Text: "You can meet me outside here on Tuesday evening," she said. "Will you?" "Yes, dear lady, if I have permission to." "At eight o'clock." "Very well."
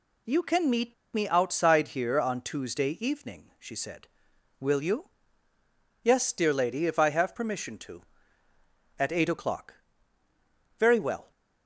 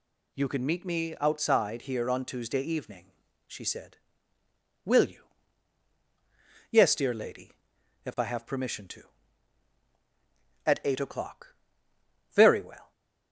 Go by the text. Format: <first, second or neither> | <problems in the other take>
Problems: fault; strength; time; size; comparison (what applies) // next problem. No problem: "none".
second | pauses between "meet" and "me"; slight; at 0.9 s; 0.20 s long